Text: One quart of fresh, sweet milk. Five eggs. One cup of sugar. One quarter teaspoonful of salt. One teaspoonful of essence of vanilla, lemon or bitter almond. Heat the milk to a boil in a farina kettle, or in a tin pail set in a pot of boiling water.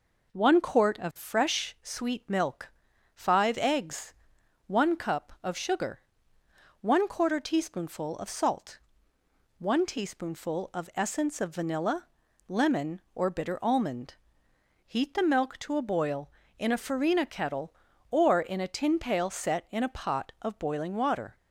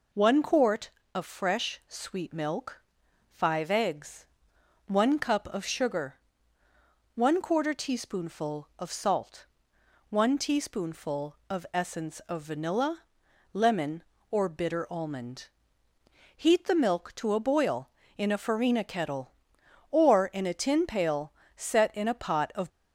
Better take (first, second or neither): first